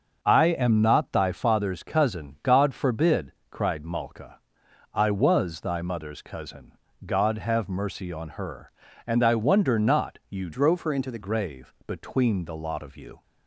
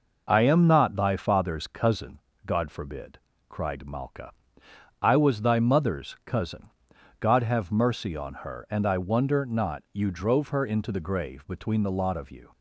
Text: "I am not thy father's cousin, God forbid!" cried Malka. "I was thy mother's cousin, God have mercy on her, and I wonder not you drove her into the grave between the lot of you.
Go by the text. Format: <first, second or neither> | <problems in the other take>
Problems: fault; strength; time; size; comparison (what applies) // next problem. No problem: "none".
second | starts louder than the rest; noticeable; until 1.2 s; 6 dB // changes voice from "drove" to "the"; from 10.5 to 11.1 s; 0.6 s long